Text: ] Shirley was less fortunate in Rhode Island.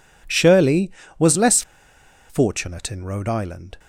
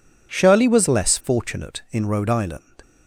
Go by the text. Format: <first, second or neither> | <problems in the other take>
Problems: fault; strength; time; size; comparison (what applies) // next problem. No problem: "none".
second | pauses between "less" and "fortunate"; noticeable; at 1.6 s; 0.67 s long